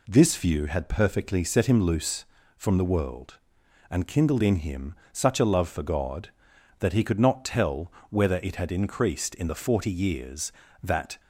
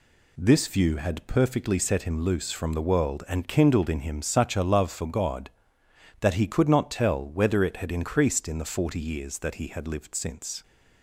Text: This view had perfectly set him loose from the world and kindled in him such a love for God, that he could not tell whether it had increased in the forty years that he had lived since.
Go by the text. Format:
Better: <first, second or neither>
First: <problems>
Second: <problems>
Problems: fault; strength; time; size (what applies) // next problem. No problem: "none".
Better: second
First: pauses between "him" and "such"; slight; at 4.9 s; 0.18 s long // pauses between "tell" and "whether"; slight; at 7.9 s; 0.18 s long // stops before "he had lived since"; at 11.1 s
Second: none